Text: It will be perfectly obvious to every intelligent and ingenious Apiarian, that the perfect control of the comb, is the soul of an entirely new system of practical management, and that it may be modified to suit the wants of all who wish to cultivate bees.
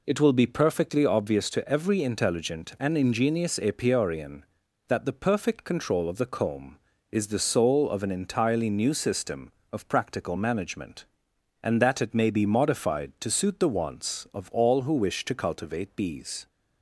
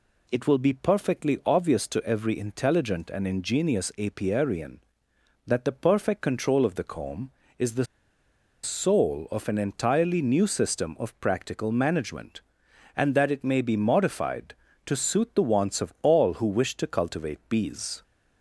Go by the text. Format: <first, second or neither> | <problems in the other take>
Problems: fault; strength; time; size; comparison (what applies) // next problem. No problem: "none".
first | pauses between "the" and "soul"; noticeable; at 7.8 s; 0.78 s long